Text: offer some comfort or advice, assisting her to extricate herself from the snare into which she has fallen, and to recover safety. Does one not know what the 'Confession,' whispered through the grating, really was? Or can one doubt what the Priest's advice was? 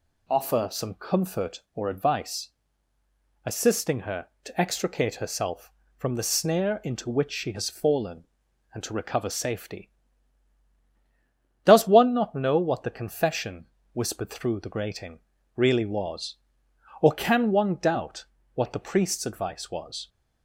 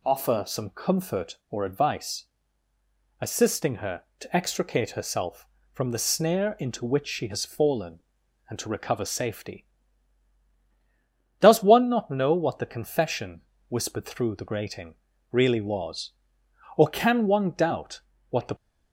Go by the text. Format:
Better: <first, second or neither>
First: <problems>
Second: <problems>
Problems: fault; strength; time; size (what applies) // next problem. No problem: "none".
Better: first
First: pauses between "doubt" and "what"; slight; at 18.2 s; 0.30 s long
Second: pauses between "doubt" and "what"; slight; at 18.0 s; 0.30 s long // stops before "Priest's advice was"; at 18.5 s